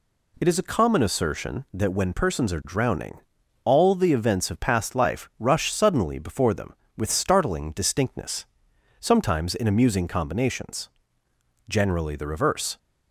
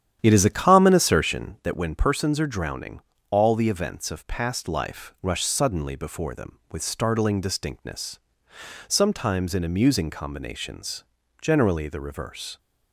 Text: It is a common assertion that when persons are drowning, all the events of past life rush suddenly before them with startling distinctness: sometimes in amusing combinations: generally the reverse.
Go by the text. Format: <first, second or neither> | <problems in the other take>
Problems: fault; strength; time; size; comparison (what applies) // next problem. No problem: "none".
first | starts louder than the rest; strong; until 1.7 s; 10 dB